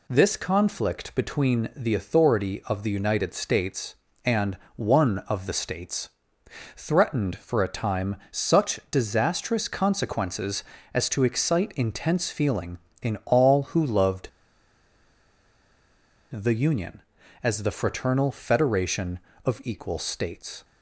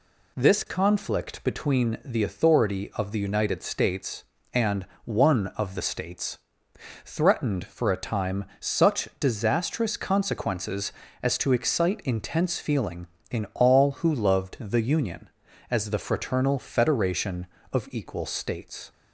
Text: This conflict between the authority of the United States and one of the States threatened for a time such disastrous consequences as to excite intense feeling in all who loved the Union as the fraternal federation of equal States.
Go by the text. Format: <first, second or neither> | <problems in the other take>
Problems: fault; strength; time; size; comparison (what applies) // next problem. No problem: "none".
second | pauses between "and" and "one"; slight; at 4.5 s; 0.18 s long; slight in the second // pauses between "States" and "threatened"; noticeable; at 6.0 s; 0.66 s long; noticeable in the second // pauses between "time" and "such"; slight; at 8.1 s; 0.16 s long; slight in the second // pauses between "loved" and "the"; strong; at 14.2 s; 2.0 s long